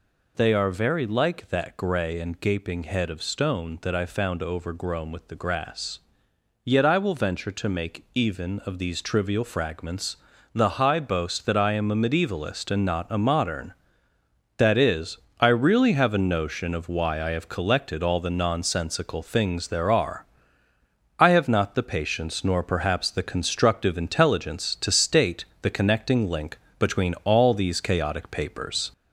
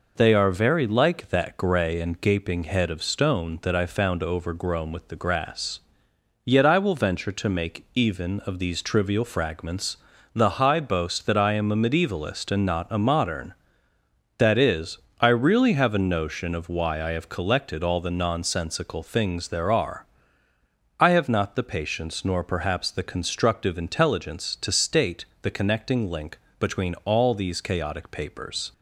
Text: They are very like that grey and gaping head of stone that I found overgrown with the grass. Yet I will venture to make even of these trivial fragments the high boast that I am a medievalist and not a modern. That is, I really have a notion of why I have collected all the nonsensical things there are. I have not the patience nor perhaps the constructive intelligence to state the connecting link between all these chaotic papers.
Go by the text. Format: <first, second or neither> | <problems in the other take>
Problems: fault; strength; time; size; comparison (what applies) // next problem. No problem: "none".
second | gets louder; slight; throughout; 3 dB // pauses between "fragments" and "the"; at 10.1 s; 0.38 s long; also in the second // pauses between "state" and "the"; slight; at 25.4 s; 0.16 s long; slight in the second // pauses between "link" and "between"; slight; at 26.5 s; 0.20 s long; slight in the second